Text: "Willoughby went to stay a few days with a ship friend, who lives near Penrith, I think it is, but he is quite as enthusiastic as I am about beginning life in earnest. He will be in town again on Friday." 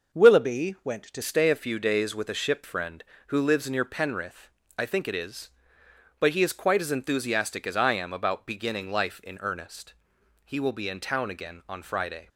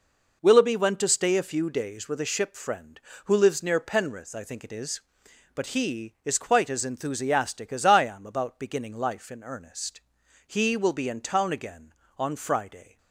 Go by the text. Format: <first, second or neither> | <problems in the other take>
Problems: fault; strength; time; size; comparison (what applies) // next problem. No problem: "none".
second | changes voice at "stay"; from 1.2 s on; 11.0 s long